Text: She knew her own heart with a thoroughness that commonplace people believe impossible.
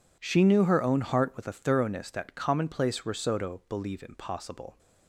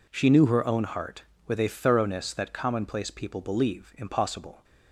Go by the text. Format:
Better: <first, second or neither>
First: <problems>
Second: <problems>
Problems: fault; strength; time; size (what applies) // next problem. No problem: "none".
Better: second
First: says "risotto" for "people"; at 3.0 s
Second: none